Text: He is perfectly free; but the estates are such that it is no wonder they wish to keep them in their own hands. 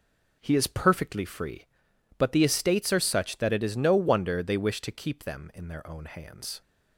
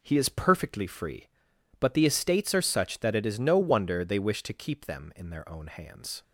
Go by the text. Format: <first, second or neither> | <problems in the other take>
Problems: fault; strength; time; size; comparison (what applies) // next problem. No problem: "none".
neither | none